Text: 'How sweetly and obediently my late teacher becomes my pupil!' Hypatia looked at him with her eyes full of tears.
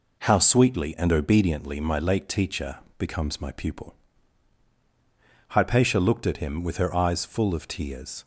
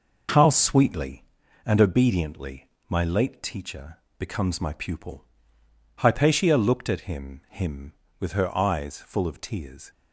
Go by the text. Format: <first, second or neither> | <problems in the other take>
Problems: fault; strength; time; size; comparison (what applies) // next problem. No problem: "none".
first | pauses between "obediently" and "my"; slight; at 2.6 s; 0.18 s long // pauses between "teacher" and "becomes"; slight; at 3.9 s; 0.22 s long; slight in the first // says "him" twice; at 7.4 s